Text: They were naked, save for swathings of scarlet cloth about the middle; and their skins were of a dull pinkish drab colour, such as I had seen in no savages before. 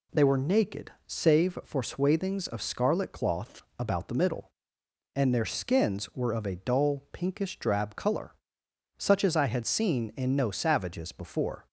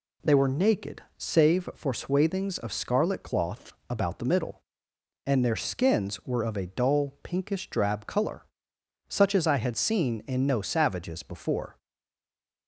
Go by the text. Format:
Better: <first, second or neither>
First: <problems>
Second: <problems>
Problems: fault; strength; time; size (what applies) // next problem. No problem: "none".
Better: first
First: pauses between "cloth" and "about"; slight; at 3.6 s; 0.16 s long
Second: pauses between "cloth" and "about"; slight; at 3.7 s; 0.16 s long // stays silent after the last word; slight; from 11.7 s on; 0.9 s long